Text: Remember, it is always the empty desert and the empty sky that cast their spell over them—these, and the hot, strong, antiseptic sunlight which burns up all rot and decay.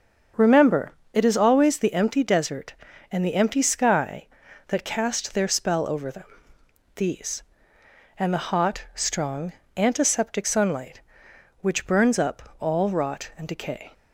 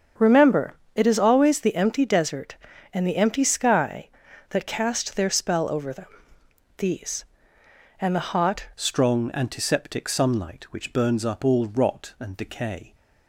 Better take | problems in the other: first | starts louder than the rest; strong; until 1.4 s; 7 dB; also in the first // changes voice at "strong"; from 8.7 s on; 4.2 s long

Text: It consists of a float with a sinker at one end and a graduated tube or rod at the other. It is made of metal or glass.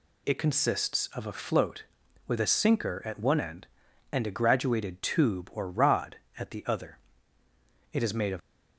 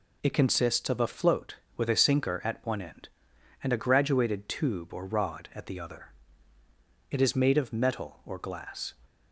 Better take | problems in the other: second | stops before "metal or glass"; at 8.4 s

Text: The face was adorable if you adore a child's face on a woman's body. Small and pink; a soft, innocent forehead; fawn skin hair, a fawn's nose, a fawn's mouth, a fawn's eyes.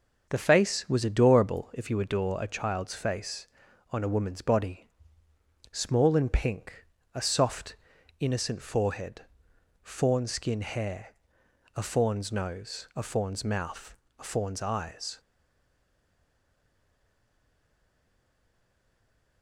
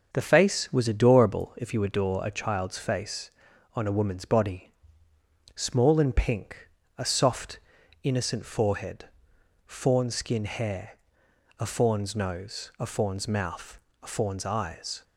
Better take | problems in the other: second | starts louder than the rest; noticeable; until 1.3 s; 6 dB; also in the second // stays silent after the last word; strong; from 15.1 s on; 4.3 s long

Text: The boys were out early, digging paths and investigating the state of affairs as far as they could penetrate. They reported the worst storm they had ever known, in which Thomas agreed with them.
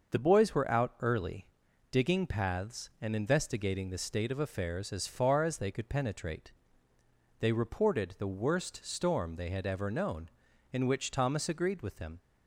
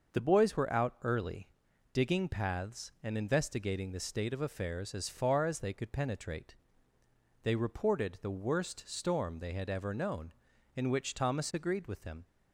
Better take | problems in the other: neither | starts louder than the rest; the same in both

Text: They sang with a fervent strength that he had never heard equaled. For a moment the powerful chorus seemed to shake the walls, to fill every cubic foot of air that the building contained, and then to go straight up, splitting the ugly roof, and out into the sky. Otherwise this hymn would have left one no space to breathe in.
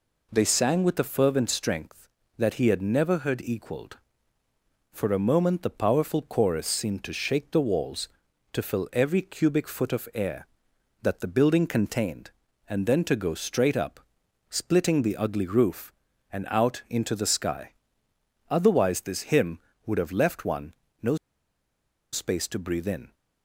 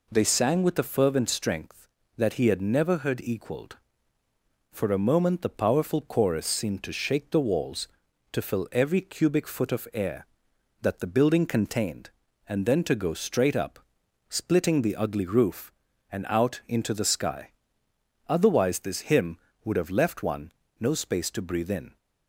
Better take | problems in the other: second | pauses between "one" and "no"; slight; at 20.7 s; 0.28 s long; slight in the second // pauses between "no" and "space"; noticeable; at 21.1 s; 0.96 s long

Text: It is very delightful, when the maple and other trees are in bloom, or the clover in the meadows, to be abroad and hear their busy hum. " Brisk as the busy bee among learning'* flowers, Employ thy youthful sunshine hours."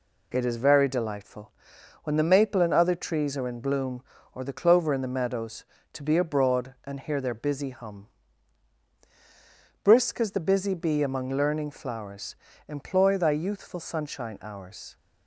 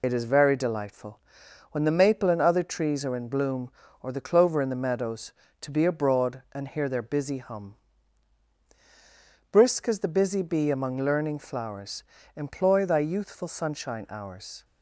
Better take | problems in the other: first | loses the start of "It"; at 0.0 s; 45 ms

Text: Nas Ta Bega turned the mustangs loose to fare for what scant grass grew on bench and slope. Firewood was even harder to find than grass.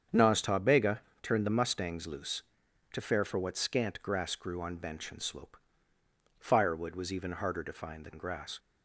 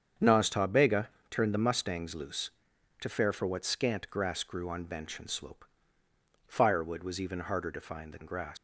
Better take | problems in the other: first | starts louder than the rest; strong; until 1.3 s; 7.5 dB; strong in the first // pauses between "Bega" and "turned"; slight; at 1.0 s; 0.20 s long; slight in the first // leaves "grass" unfinished; at 8.5 s; 90 ms

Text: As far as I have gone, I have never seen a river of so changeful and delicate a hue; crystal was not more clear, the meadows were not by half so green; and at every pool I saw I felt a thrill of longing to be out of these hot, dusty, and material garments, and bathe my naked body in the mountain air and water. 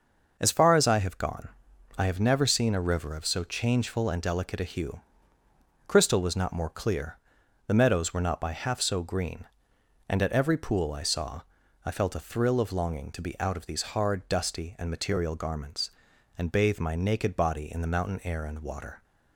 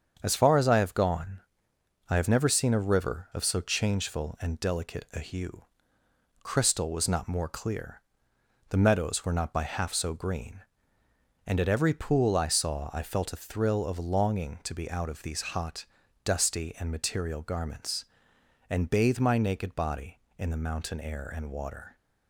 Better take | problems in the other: second | starts louder than the rest; noticeable; until 1.4 s; 6 dB; strong in the second // pauses between "saw" and "I"; at 11.4 s; 0.44 s long // says "hard" for "hot"; at 13.9 s

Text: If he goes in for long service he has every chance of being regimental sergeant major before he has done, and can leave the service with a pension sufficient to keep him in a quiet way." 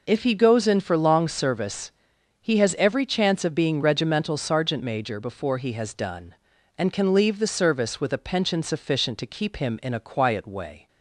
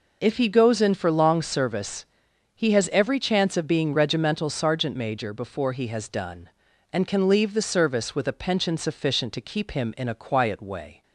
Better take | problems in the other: neither | pauses between "service" and "he"; noticeable; the same in both

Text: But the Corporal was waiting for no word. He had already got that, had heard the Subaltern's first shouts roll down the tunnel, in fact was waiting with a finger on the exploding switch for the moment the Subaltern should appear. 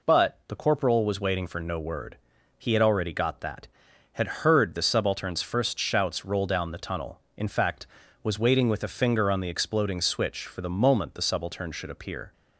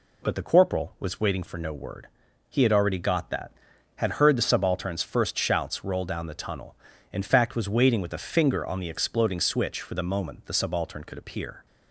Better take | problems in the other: first | says "could" for "should"; at 11.0 s

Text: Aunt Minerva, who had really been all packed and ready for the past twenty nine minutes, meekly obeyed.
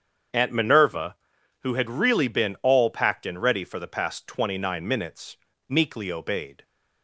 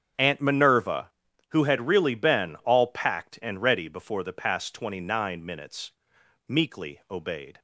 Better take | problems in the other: first | starts louder than the rest; strong; until 1.5 s; 7.5 dB; strong in the first // says "before" for "for"; at 3.8 s

